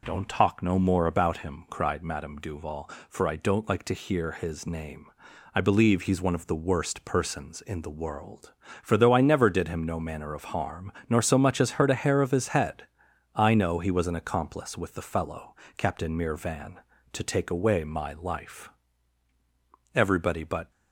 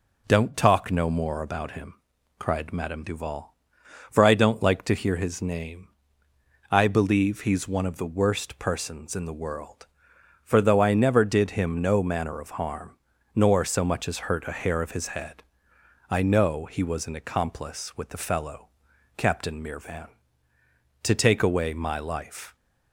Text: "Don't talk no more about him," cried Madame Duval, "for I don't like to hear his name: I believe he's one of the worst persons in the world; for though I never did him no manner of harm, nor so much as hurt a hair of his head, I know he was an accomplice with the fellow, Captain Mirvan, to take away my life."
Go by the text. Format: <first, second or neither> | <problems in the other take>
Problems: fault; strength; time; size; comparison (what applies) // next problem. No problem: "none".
second | goes on to say "Everybody but"; noticeable; from 19.9 s on; 0.76 s long